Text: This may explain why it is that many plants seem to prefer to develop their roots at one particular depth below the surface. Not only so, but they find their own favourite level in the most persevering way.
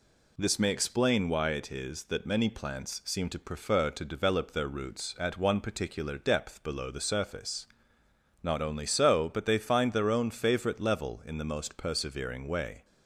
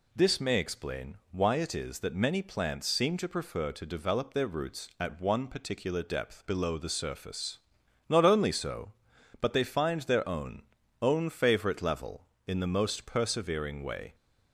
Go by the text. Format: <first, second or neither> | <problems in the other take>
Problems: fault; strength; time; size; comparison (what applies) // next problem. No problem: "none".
first | pauses between "explain" and "why"; slight; at 1.1 s; 0.15 s long // says "own" twice; at 11.0 s